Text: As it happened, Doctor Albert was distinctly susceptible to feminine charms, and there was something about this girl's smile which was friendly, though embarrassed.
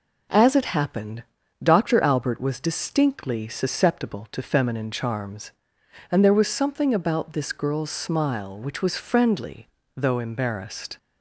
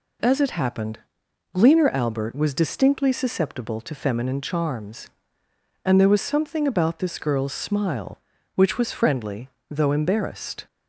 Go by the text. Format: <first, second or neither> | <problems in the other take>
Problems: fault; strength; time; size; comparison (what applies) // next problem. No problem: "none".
first | says "Gleaner" for "Doctor"; at 1.5 s